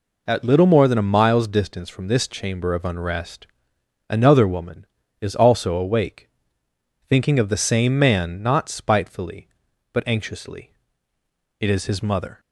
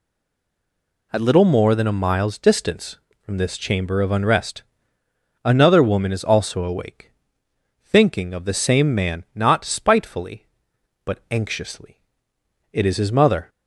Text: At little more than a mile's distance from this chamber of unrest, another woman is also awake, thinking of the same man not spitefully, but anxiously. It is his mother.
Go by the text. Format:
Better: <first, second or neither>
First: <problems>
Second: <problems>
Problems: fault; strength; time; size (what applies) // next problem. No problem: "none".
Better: first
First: none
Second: stays silent before the first word; until 1.1 s; 1.1 s long